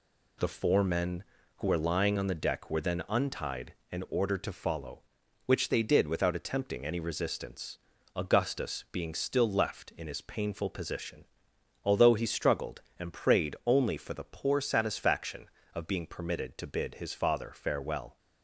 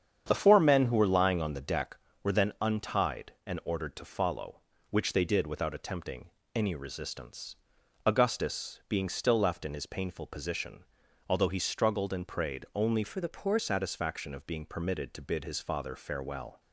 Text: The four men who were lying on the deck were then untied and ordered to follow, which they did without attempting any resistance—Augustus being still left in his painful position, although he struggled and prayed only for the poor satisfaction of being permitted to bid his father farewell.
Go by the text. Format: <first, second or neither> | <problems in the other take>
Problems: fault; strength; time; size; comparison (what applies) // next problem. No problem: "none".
first | starts louder than the rest; strong; until 1.2 s; 8.5 dB // pauses between "attempting" and "any"; slight; at 6.3 s; 0.22 s long // changes voice from "for" to "poor"; from 13.0 to 13.5 s; 0.5 s long